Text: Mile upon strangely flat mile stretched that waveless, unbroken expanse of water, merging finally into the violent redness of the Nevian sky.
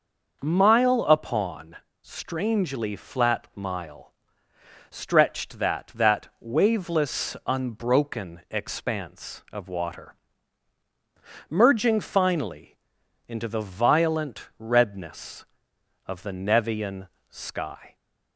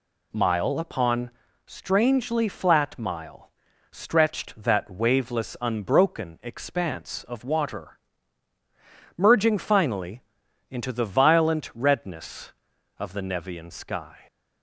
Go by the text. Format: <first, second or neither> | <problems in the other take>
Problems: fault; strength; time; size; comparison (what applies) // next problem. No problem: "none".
second | pauses between "upon" and "strangely"; slight; at 1.7 s; 0.26 s long; slight in the second // pauses between "mile" and "stretched"; noticeable; at 4.1 s; 0.76 s long; also in the second // says "that" twice; at 5.9 s // pauses between "finally" and "into"; noticeable; at 12.7 s; 0.50 s long; noticeable in the second // pauses between "Nevian" and "sky"; slight; at 17.0 s; 0.20 s long